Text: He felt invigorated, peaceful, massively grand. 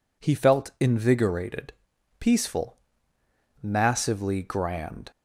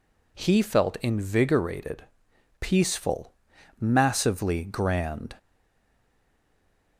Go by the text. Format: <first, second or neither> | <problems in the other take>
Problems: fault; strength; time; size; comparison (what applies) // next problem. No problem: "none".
first | stays silent after the last word; noticeable; from 5.3 s on; 1.6 s long